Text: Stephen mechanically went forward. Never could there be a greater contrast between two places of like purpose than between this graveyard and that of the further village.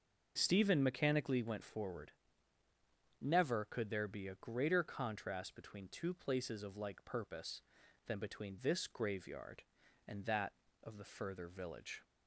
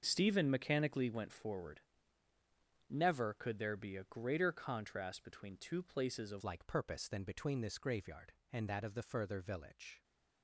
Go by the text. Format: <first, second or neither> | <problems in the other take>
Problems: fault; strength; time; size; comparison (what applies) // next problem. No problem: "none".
first | starts louder than the rest; until 1.0 s; 6 dB // changes voice at "like"; from 6.4 s on; 3.6 s long